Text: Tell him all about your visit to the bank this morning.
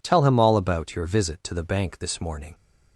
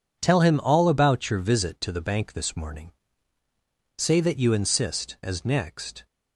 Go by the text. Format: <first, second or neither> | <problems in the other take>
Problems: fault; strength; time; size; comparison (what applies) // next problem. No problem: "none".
first | goes on to say "Say that you insist as next"; strong; from 3.9 s on; 2.1 s long